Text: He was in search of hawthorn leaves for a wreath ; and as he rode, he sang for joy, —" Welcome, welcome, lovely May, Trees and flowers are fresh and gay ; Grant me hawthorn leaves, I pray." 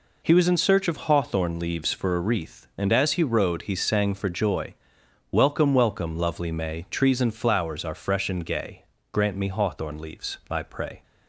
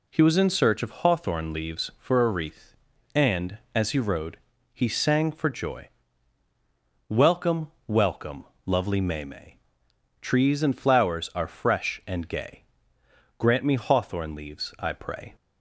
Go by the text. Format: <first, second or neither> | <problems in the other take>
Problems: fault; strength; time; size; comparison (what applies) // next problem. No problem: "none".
first | says "May" twice; at 9.2 s